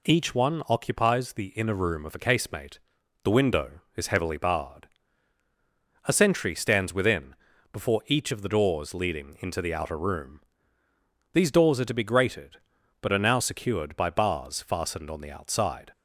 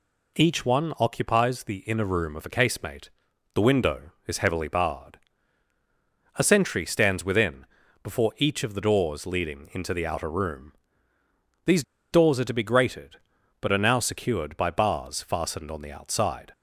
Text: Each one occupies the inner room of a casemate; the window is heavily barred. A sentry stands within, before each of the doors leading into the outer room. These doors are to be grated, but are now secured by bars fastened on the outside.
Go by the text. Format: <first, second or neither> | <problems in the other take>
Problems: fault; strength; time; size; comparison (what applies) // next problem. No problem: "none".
first | pauses between "These" and "doors"; slight; at 11.8 s; 0.28 s long